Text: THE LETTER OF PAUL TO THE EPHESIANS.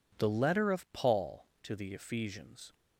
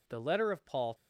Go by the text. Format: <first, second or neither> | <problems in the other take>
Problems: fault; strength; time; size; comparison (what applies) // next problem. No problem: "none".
first | stops before "TO THE EPHESIANS"; at 0.9 s